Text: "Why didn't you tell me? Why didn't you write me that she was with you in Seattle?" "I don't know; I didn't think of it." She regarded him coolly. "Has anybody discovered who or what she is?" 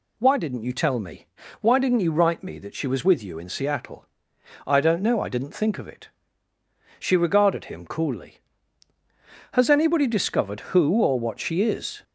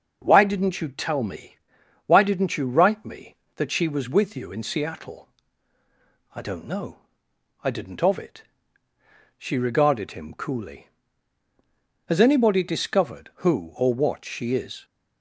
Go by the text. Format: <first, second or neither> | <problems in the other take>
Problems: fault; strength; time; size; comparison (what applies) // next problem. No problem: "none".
first | starts louder than the rest; noticeable; until 1.2 s; 6 dB // skips "think"; at 8.0 s